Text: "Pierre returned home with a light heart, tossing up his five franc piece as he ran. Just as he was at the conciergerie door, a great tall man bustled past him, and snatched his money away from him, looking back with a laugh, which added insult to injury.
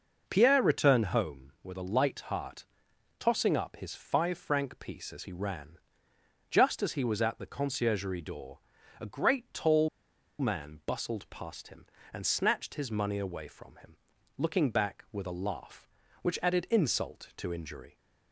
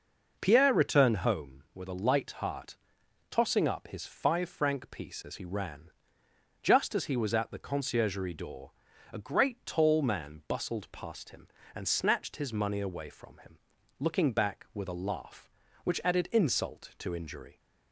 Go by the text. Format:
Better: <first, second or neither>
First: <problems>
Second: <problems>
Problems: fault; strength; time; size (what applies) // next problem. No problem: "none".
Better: second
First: pauses between "tall" and "man"; noticeable; at 9.8 s; 0.52 s long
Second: none